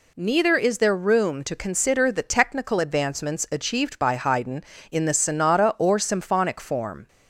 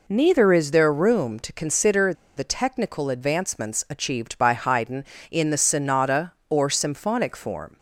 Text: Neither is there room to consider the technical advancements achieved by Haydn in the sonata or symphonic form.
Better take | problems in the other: first | pauses between "consider" and "the"; slight; at 2.1 s; 0.23 s long

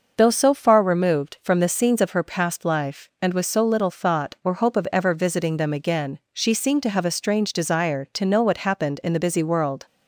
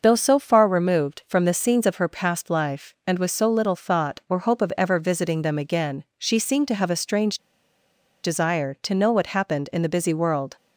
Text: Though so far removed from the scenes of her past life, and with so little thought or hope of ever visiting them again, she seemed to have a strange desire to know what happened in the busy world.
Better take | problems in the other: first | pauses between "strange" and "desire"; noticeable; at 7.3 s; 0.84 s long

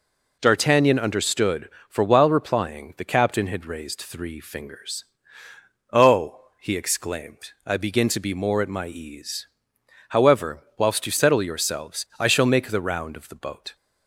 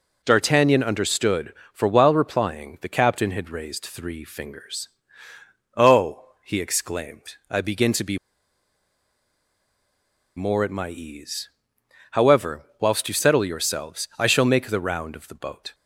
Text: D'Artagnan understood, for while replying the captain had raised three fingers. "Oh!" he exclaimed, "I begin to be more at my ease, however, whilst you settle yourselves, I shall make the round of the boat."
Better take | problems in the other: first | pauses between "be" and "more"; strong; at 8.1 s; 2.1 s long

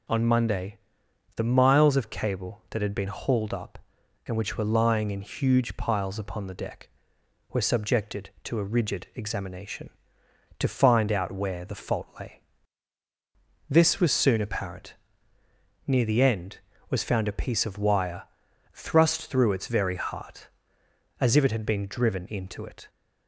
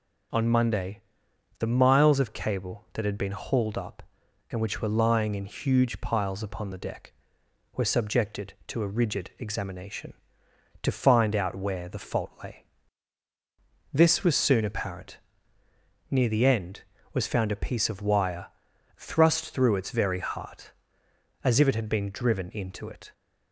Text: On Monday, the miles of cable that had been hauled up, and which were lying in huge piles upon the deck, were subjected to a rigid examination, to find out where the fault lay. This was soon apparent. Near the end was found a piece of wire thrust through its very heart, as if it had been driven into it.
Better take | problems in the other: neither | pauses between "wire" and "thrust"; noticeable; the same in both

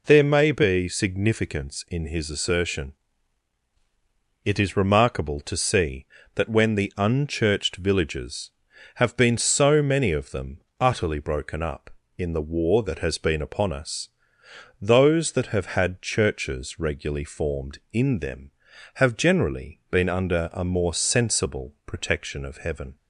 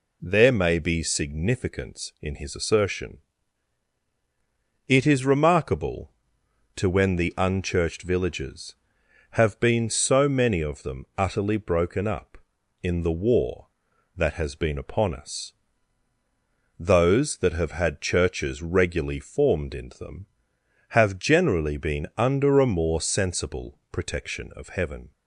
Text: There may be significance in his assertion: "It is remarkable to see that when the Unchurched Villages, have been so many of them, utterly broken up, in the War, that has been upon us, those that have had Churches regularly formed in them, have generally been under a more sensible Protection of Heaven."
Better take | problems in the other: first | skips "see that"; at 6.8 s

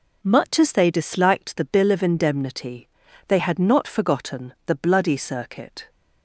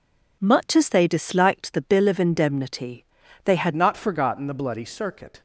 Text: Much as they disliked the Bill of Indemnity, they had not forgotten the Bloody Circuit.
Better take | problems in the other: first | changes voice at "not"; from 3.7 s on; 1.7 s long

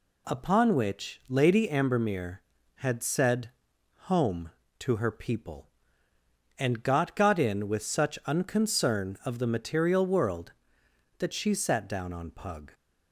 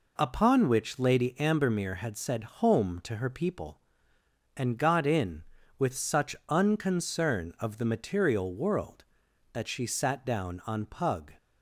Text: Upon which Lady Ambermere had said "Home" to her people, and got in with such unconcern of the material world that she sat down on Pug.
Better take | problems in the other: second | pauses between "said" and "Home"; noticeable; at 3.5 s; 0.58 s long // says "got" twice; at 7.1 s

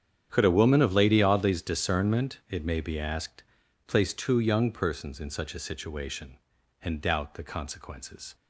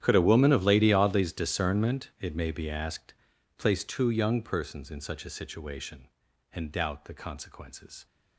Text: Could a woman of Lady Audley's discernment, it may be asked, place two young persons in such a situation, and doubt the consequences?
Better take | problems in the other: first | gets quieter; strong; throughout; 20 dB // starts louder than the rest; strong; until 1.0 s; 10.5 dB; strong in the first

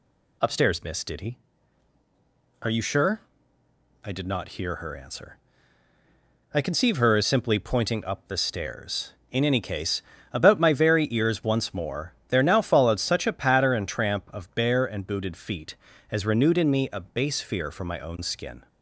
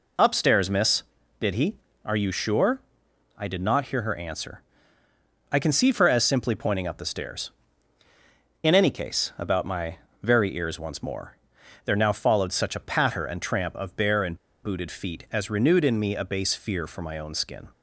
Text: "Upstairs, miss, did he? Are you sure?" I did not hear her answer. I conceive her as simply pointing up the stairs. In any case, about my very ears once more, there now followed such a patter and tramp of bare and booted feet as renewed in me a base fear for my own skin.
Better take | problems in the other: first | pauses between "my" and "very"; slight; at 9.9 s; 0.26 s long // pauses between "and" and "booted"; slight; at 14.3 s; 0.27 s long

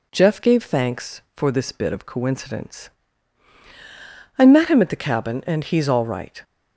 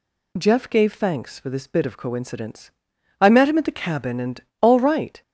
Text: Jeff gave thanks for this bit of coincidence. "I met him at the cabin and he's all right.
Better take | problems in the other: first | skips "he's"; at 4.5 s

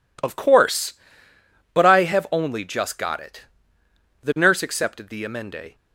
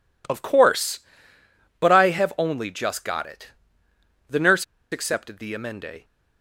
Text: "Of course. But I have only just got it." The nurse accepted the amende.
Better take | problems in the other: first | pauses between "nurse" and "accepted"; slight; at 4.6 s; 0.27 s long

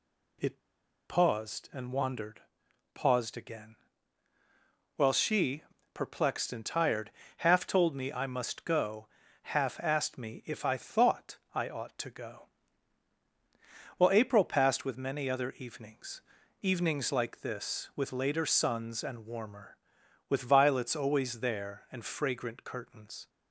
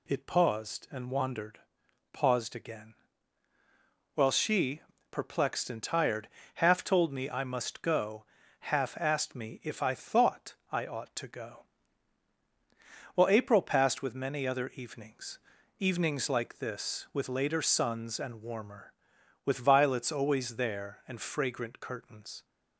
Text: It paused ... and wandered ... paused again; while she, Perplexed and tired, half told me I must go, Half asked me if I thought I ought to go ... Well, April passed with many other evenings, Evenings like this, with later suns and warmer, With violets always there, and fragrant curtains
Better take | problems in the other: second | pauses between "It" and "paused"; noticeable; at 0.5 s; 0.49 s long // pauses between "thought" and "I"; slight; at 11.3 s; 0.16 s long; slight in the second

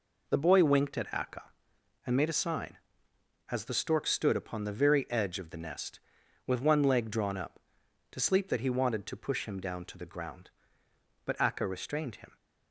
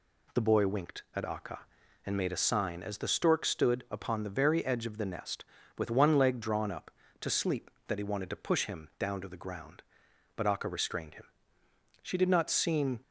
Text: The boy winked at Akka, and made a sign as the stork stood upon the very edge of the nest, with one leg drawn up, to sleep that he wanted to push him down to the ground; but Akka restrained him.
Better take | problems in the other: first | goes on to say "She did not seem"; noticeable; from 12.0 s on; 0.96 s long

